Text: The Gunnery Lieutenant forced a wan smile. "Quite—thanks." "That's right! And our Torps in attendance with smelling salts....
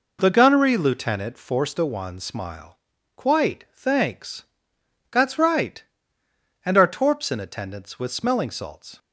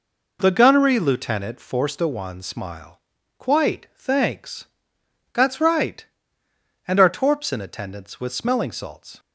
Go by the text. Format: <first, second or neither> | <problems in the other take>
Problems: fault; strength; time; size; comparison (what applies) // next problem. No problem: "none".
neither | none